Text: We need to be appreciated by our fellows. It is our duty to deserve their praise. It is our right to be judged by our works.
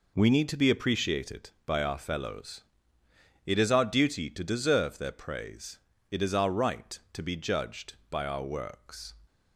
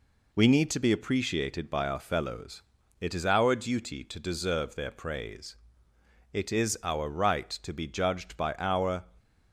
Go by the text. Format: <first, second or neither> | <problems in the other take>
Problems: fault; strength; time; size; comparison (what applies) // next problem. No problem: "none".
first | stops before "works"; at 9.1 s